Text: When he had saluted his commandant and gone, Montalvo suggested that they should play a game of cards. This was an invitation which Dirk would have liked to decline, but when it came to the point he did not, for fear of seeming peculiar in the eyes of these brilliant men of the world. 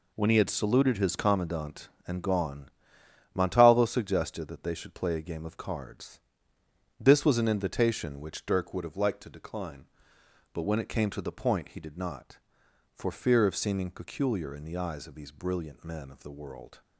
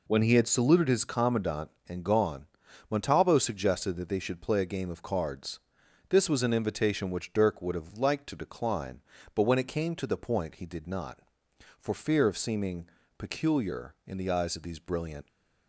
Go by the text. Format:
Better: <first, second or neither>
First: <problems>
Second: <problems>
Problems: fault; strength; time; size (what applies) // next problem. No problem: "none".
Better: first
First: none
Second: pauses between "seeming" and "peculiar"; slight; at 12.8 s; 0.30 s long // stops before "men of the world"; at 15.2 s